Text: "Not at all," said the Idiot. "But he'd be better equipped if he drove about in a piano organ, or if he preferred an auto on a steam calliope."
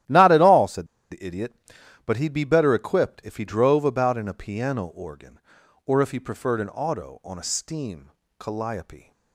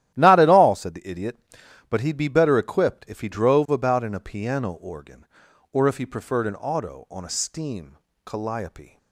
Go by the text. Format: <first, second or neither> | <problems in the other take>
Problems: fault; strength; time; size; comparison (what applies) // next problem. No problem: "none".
second | starts louder than the rest; strong; until 1.3 s; 13 dB; strong in the second // pauses between "said" and "the"; slight; at 0.8 s; 0.25 s long // pauses between "steam" and "calliope"; slight; at 8.1 s; 0.28 s long; slight in the second